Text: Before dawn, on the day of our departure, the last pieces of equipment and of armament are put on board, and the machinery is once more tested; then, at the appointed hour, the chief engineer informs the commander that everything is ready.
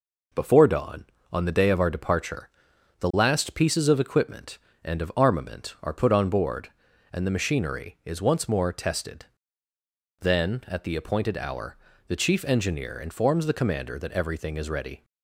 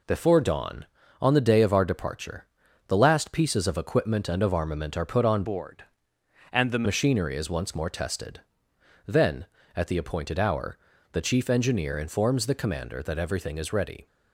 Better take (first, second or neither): first